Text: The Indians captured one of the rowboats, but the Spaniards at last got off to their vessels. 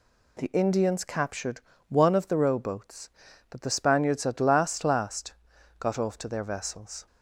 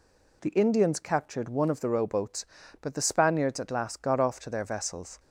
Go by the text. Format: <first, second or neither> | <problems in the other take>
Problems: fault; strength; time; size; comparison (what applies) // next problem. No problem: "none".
second | pauses between "captured" and "one"; slight; at 1.6 s; 0.26 s long // says "last" twice; at 4.8 s